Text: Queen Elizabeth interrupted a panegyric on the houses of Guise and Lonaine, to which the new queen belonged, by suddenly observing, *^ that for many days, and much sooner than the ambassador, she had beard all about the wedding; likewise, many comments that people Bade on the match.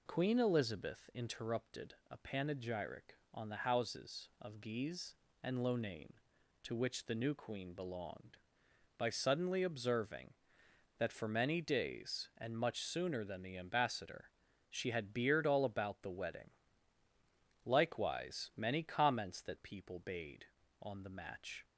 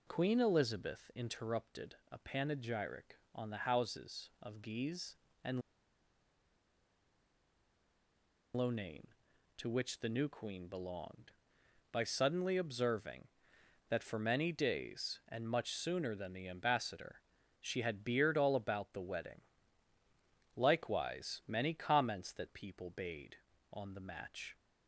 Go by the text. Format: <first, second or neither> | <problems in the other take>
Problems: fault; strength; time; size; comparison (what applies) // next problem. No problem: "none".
first | pauses between "and" and "Lonaine"; strong; at 5.6 s; 2.9 s long